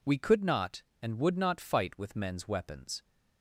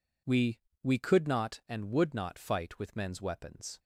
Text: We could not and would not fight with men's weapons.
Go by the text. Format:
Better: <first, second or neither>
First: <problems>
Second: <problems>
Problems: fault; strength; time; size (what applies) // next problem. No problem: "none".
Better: first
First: none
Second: says "We" twice; at 0.8 s